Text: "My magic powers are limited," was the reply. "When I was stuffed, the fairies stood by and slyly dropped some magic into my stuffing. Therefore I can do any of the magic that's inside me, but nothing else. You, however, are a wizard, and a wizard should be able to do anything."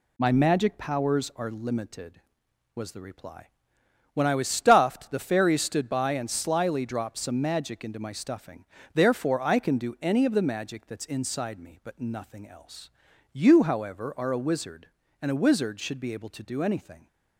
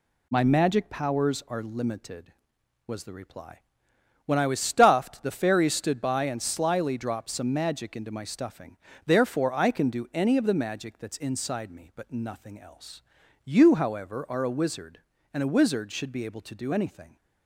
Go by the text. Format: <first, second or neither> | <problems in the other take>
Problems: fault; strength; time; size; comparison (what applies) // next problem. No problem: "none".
neither | none